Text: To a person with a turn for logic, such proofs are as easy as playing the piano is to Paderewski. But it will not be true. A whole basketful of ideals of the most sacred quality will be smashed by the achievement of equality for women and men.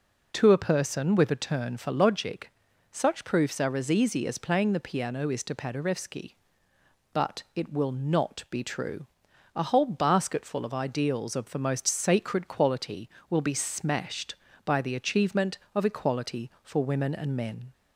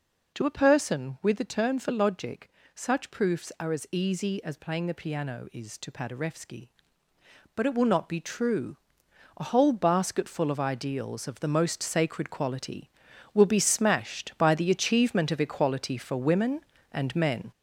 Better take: first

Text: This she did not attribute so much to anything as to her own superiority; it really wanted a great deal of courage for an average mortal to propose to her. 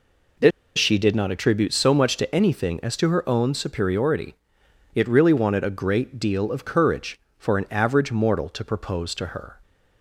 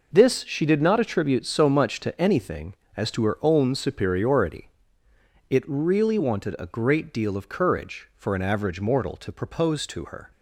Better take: second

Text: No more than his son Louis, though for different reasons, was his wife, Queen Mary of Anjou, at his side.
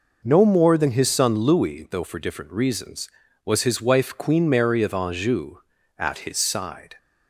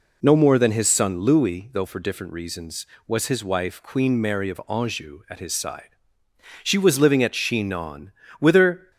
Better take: first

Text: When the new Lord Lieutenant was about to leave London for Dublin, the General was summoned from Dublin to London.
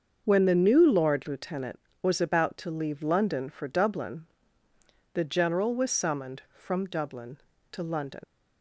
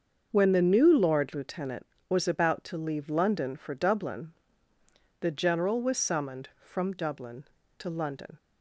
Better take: second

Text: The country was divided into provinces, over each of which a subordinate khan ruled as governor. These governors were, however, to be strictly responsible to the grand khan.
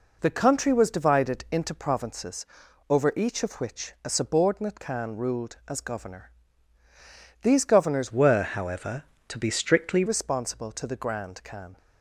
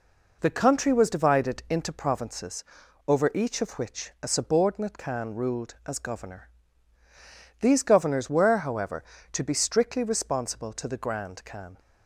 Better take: second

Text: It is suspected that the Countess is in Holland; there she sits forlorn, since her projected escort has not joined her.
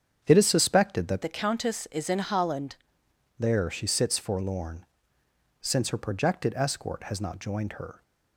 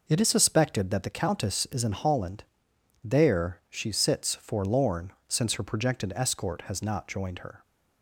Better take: second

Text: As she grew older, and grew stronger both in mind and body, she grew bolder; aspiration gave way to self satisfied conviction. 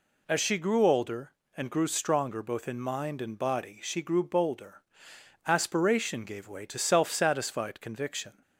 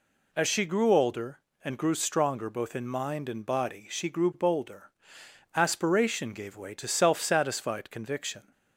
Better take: neither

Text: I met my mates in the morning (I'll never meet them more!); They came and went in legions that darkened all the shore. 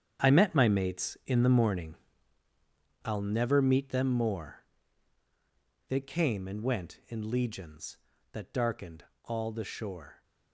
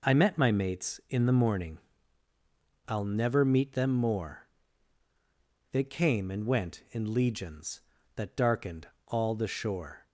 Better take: second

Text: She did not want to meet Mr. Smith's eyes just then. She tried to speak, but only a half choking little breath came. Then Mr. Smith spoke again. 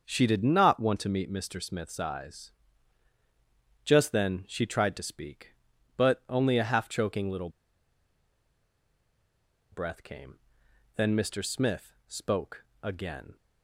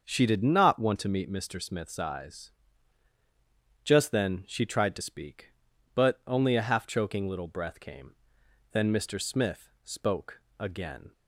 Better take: second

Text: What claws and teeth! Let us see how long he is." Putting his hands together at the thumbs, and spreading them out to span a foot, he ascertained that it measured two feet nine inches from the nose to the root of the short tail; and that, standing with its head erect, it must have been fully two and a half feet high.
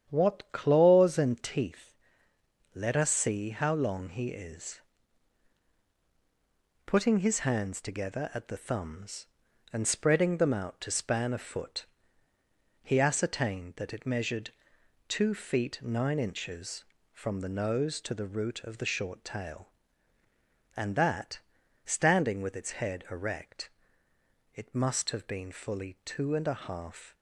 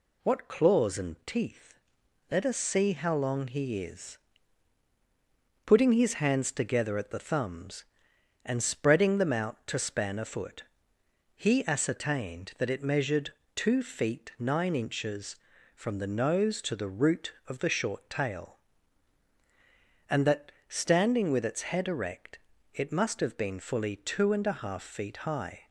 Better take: second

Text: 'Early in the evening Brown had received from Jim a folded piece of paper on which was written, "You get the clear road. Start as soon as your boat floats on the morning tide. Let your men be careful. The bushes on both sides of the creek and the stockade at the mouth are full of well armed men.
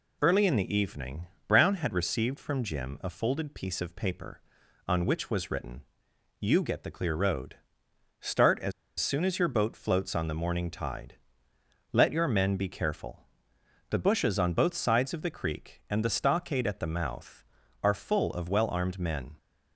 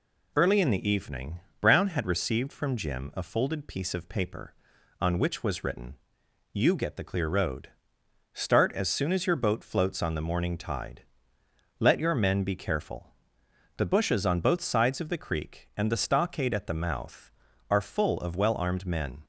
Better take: second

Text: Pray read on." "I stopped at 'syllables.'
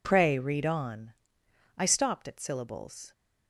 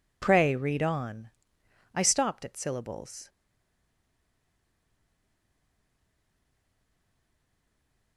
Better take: first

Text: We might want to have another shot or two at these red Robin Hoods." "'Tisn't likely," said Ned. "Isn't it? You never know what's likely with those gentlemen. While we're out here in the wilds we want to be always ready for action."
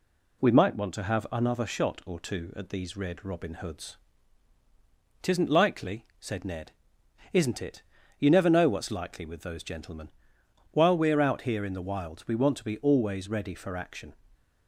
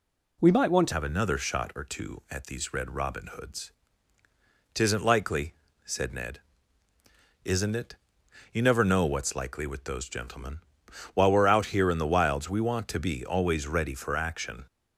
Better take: first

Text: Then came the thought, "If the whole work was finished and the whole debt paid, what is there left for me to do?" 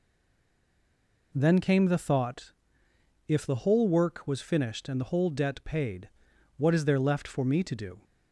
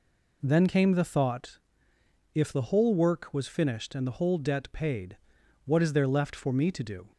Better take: second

